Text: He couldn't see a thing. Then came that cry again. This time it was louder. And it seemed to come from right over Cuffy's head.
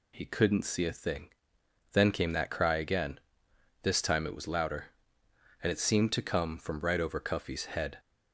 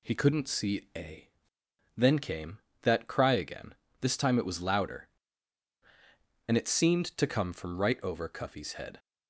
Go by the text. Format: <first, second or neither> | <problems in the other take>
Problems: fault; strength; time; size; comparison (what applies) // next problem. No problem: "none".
first | skips "thing"; at 1.6 s